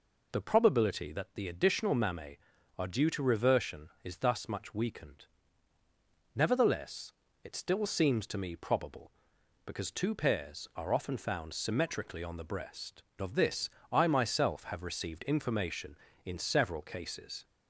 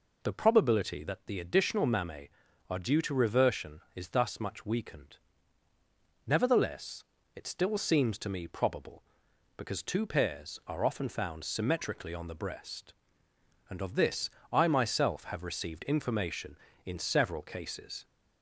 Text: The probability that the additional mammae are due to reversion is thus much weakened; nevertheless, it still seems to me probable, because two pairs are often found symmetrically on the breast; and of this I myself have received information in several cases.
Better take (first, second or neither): second